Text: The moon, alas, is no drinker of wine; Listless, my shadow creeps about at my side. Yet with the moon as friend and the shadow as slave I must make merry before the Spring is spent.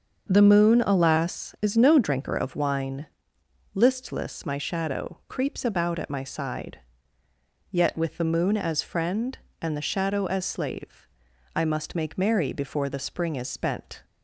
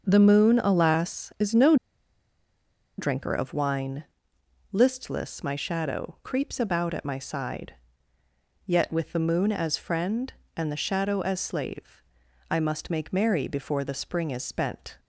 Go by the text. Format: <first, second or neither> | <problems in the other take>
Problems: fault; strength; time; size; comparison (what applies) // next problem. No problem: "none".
first | starts louder than the rest; until 1.1 s; 6.5 dB; also in the first // pauses between "no" and "drinker"; at 1.7 s; 1.2 s long // pauses between "slave" and "I"; noticeable; at 12.0 s; 0.48 s long; noticeable in the first